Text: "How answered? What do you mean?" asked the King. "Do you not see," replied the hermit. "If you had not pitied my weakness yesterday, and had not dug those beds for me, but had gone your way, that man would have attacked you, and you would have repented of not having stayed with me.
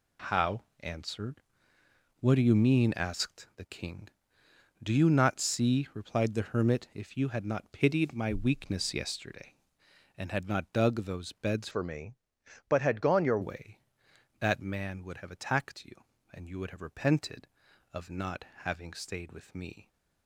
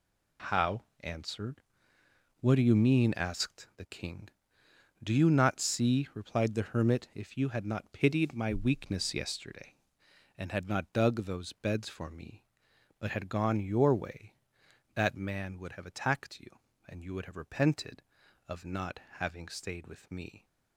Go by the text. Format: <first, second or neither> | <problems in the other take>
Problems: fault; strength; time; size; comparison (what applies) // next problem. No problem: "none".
second | pauses between "How" and "answered"; slight; at 0.6 s; 0.16 s long; slight in the second // changes voice from "for" to "your"; from 11.7 to 13.3 s; 1.6 s long // pauses between "not" and "having"; slight; at 18.4 s; 0.18 s long; slight in the second